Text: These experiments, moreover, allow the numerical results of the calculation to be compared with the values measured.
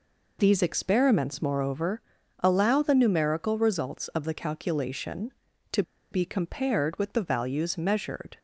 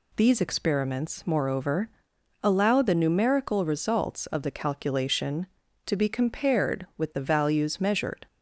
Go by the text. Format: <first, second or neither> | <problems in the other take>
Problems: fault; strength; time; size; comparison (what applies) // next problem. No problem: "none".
second | pauses between "to" and "be"; slight; at 5.8 s; 0.29 s long